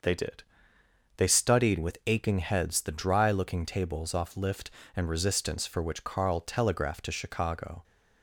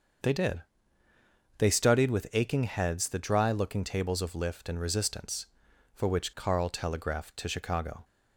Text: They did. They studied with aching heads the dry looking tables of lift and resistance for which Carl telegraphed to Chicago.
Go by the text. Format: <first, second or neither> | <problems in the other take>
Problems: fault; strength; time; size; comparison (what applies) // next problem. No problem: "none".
second | starts louder than the rest; until 1.7 s; 6.5 dB; also in the second // says "off" for "of"; at 4.1 s